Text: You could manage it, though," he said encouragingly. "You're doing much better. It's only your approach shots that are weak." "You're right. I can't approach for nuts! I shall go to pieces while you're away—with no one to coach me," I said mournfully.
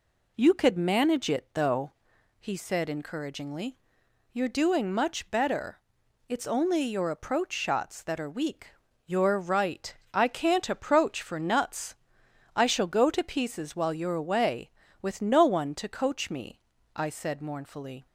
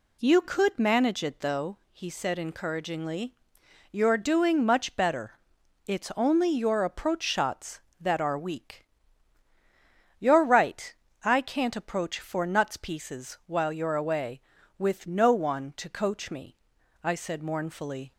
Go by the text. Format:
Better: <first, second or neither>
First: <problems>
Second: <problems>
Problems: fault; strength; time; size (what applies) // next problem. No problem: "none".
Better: first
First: none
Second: skips "I shall go to"; at 12.7 s